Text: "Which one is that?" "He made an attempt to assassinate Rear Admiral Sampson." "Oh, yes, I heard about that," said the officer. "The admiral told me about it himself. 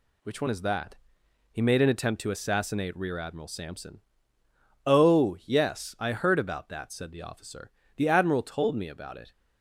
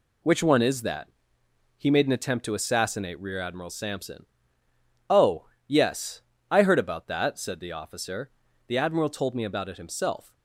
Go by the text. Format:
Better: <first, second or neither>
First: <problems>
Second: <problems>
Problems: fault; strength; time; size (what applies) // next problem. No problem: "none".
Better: second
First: stops before "himself"; at 9.3 s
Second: none